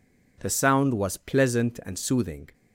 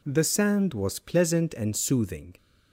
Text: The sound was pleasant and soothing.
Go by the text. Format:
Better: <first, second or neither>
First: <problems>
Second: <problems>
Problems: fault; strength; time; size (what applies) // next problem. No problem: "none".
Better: first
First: none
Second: says "sand" for "sound"; at 0.2 s